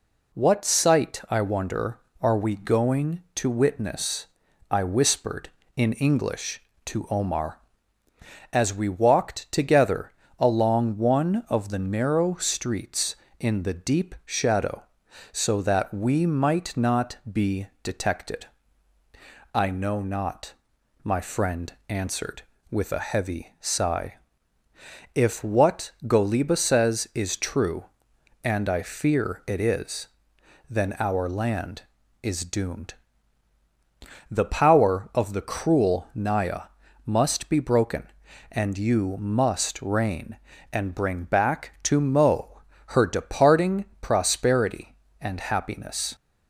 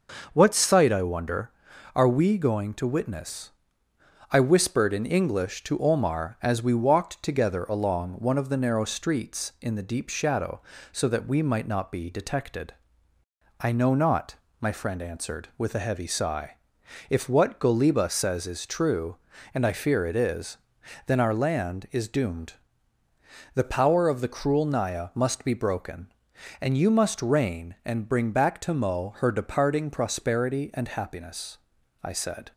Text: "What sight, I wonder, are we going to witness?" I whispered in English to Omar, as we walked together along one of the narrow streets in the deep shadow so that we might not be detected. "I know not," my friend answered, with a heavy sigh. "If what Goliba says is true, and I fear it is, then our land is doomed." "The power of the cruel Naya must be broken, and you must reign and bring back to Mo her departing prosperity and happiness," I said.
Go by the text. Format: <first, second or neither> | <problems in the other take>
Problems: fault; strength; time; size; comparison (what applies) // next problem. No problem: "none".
second | pauses between "together" and "along"; slight; at 10.1 s; 0.26 s long // pauses between "be" and "detected"; slight; at 17.6 s; 0.16 s long // pauses between "friend" and "answered"; slight; at 21.7 s; 0.16 s long // pauses between "Naya" and "must"; slight; at 36.6 s; 0.36 s long // pauses between "Mo" and "her"; slight; at 42.6 s; 0.34 s long // pauses between "departing" and "prosperity"; slight; at 43.8 s; 0.16 s long // stops before "I said"; at 46.1 s